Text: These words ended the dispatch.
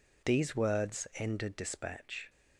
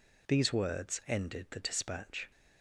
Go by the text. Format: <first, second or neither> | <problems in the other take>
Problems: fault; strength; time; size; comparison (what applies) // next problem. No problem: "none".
second | skips "the"; at 1.5 s